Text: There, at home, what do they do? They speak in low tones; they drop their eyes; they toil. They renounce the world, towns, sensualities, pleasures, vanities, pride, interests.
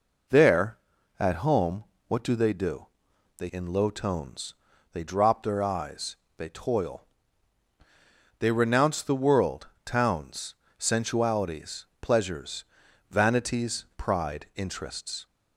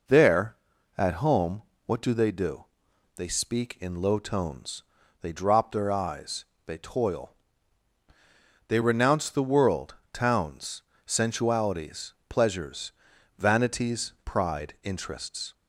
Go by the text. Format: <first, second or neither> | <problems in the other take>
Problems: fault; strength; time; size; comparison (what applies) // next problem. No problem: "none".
second | skips "speak"; at 3.5 s